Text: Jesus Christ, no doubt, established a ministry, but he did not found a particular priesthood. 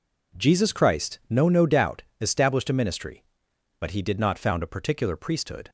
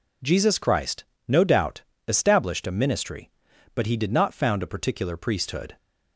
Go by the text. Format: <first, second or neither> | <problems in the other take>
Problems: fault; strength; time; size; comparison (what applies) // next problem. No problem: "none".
second | says "no" twice; at 1.4 s